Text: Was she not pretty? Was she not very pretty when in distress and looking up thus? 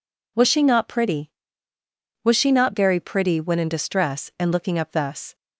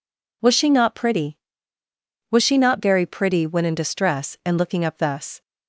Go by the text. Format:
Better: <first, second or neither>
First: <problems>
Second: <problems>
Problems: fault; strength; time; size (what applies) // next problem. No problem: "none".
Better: neither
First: none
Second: none